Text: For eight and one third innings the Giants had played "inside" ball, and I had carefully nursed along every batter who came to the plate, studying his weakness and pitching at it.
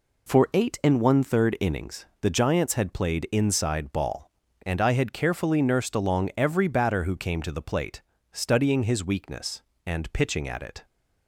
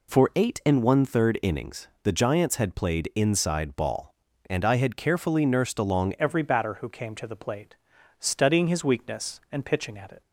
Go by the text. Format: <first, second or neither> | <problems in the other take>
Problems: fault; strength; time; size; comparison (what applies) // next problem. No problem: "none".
first | changes voice at "every"; from 6.1 s on; 4.1 s long